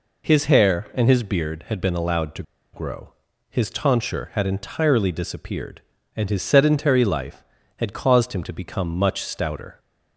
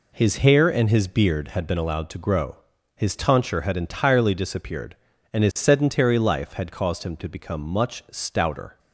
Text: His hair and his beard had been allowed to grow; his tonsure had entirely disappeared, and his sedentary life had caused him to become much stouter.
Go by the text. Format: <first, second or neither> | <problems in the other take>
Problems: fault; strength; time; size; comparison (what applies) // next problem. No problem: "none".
second | pauses between "to" and "grow"; slight; at 2.4 s; 0.30 s long